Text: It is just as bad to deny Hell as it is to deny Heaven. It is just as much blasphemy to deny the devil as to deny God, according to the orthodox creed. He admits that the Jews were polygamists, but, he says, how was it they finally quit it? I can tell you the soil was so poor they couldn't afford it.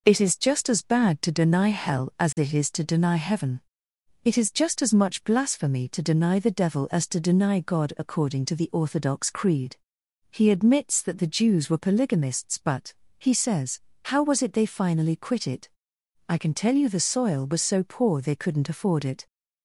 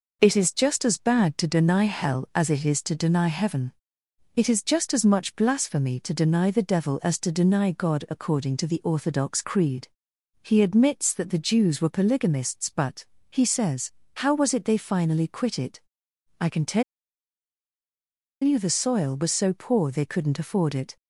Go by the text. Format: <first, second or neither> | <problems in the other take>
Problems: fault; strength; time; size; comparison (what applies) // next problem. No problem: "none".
first | pauses between "tell" and "you"; strong; at 16.8 s; 1.6 s long